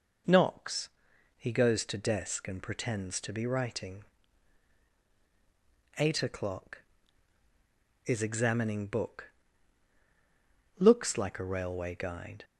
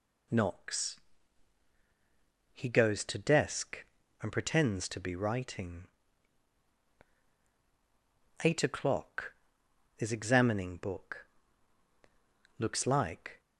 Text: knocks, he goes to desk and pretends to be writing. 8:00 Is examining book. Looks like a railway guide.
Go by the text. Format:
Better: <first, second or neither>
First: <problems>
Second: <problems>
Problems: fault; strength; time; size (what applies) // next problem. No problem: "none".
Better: first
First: none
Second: stops before "a railway guide"; at 13.3 s